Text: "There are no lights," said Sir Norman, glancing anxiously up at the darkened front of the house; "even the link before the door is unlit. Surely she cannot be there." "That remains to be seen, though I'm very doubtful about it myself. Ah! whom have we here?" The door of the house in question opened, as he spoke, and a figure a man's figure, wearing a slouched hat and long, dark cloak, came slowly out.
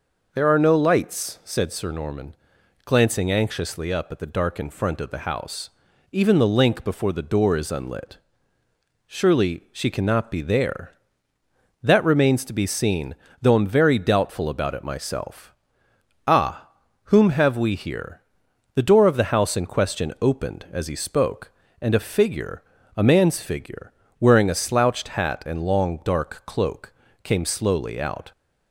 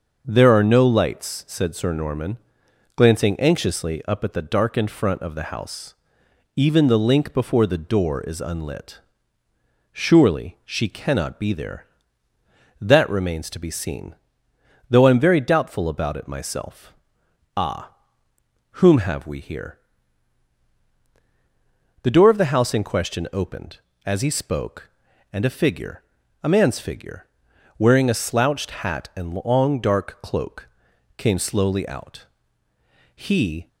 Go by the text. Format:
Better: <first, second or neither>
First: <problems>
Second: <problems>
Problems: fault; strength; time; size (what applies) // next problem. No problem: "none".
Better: first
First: pauses between "figure" and "a"; slight; at 22.6 s; 0.32 s long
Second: starts louder than the rest; noticeable; until 1.2 s; 6 dB // pauses between "figure" and "a"; at 26.0 s; 0.42 s long // goes on to say "He"; from 33.1 s on; 0.52 s long